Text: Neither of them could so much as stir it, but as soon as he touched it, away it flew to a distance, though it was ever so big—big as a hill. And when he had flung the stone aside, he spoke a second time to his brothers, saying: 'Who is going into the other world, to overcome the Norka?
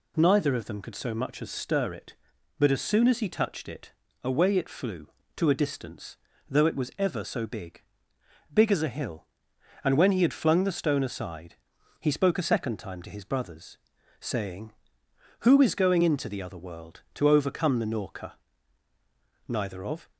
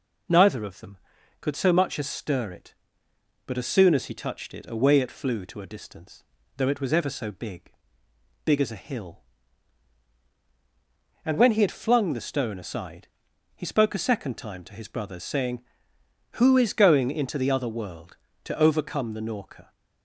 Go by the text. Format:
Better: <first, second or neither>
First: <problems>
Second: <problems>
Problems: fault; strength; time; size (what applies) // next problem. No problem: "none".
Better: second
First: goes on to say "Neither of"; noticeable; from 19.4 s on; 0.64 s long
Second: none